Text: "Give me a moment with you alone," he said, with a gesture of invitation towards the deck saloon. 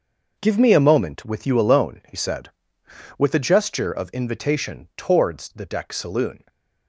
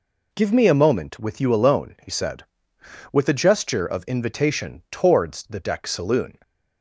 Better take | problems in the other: second | gets quieter; strong; throughout; 9 dB

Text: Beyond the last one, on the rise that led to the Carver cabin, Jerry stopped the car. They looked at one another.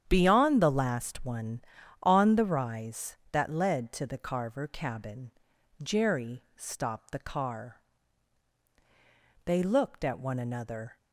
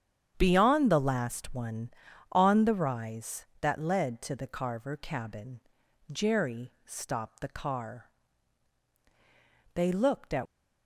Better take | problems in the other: first | starts louder than the rest; strong; until 1.3 s; 8.5 dB; strong in the first // stops before "one another"; at 10.4 s

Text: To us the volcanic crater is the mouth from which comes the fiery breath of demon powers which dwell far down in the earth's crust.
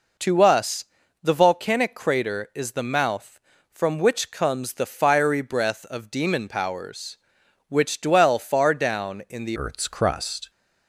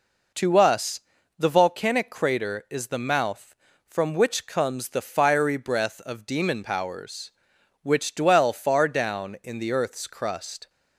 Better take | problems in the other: second | pauses between "us" and "the"; slight; at 0.8 s; 0.36 s long; slight in the second // changes voice at "earth's"; from 9.5 s on; 0.9 s long

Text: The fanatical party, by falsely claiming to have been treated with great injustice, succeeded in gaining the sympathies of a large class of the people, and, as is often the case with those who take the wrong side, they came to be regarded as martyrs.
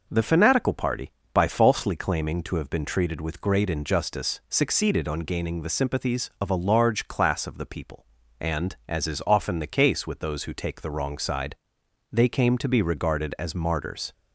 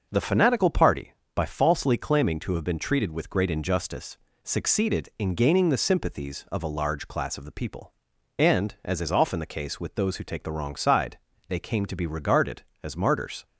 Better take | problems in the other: second | says "on" for "in"; at 5.0 s

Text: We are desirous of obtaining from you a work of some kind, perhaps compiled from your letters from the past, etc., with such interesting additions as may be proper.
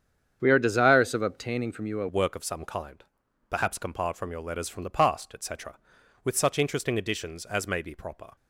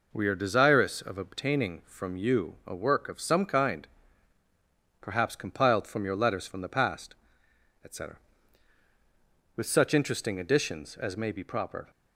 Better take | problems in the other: second | starts louder than the rest; strong; until 1.4 s; 8 dB // changes voice at "work"; from 2.0 s on; 6.3 s long

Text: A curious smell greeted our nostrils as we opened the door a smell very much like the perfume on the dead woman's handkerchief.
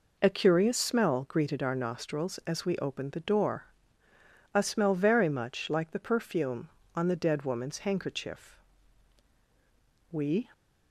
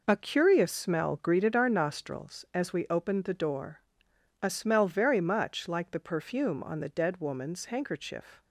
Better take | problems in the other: second | pauses between "door" and "a"; noticeable; at 3.6 s; 0.86 s long; noticeable in the second // goes on to say "We"; slight; from 10.1 s on; 0.38 s long

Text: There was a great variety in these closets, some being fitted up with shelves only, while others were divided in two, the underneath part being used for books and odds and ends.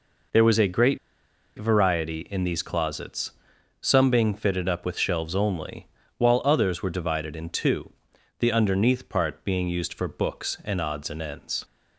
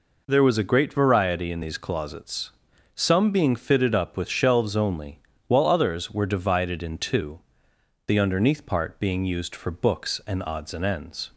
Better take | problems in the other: second | pauses between "great" and "variety"; noticeable; at 0.9 s; 0.60 s long

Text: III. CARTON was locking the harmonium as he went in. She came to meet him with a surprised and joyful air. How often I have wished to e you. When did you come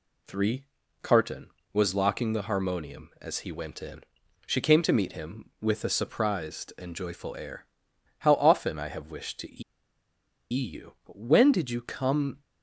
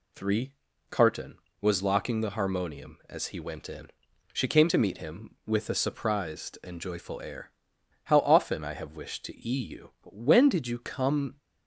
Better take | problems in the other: second | pauses between "to" and "e"; noticeable; at 9.6 s; 0.89 s long

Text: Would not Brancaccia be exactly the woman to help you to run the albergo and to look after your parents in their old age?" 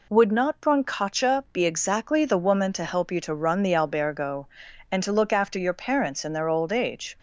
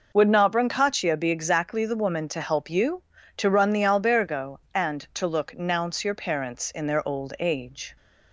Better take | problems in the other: first | says "nounce" for "after"; at 5.5 s

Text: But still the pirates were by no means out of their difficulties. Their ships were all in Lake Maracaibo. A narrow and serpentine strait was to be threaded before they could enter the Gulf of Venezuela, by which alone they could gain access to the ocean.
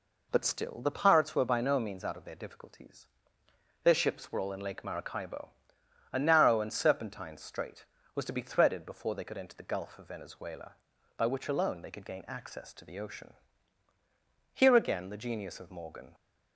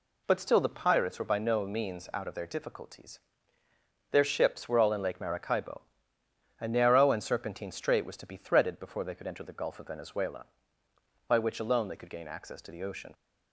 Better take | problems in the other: second | goes on to say "Here again the genius of Morgan"; from 14.5 s on; 1.6 s long

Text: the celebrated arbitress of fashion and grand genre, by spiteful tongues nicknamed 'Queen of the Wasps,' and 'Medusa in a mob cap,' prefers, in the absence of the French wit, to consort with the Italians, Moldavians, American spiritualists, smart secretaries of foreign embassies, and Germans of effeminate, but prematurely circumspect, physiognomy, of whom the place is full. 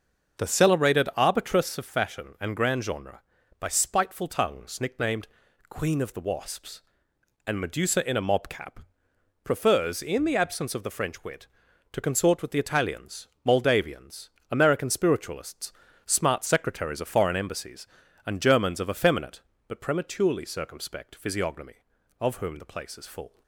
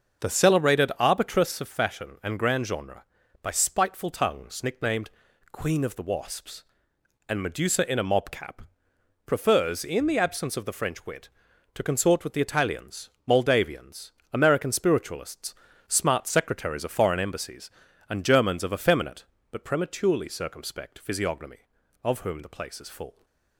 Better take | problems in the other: neither | starts louder than the rest; the same in both // pauses between "nicknamed" and "Queen"; the same in both

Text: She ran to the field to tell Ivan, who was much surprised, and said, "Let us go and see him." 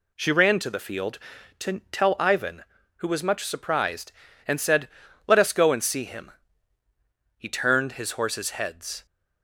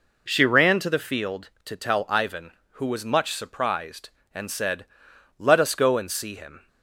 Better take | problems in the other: second | goes on to say "He turned his horses heads"; strong; from 7.3 s on; 1.6 s long

